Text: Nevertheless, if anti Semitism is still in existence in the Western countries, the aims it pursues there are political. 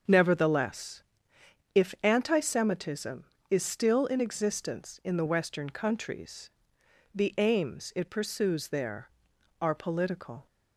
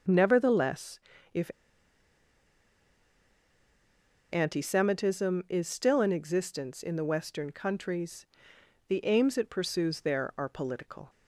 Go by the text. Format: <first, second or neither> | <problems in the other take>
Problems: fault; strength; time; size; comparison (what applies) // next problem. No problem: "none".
first | starts louder than the rest; until 1.3 s; 6.5 dB; strong in the first // pauses between "if" and "anti"; strong; at 1.5 s; 2.8 s long